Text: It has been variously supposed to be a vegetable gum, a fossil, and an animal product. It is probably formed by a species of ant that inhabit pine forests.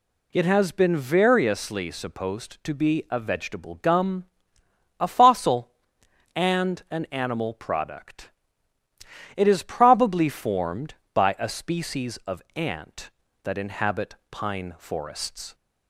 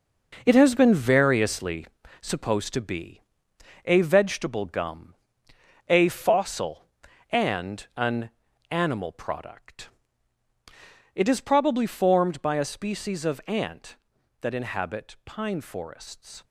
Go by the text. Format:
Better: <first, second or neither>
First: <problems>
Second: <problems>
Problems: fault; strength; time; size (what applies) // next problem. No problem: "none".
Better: first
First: none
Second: gets quieter; strong; throughout; 9 dB // pauses between "variously" and "supposed"; slight; at 1.8 s; 0.36 s long // pauses between "be" and "a"; noticeable; at 3.2 s; 0.64 s long // pauses between "an" and "animal"; at 8.2 s; 0.40 s long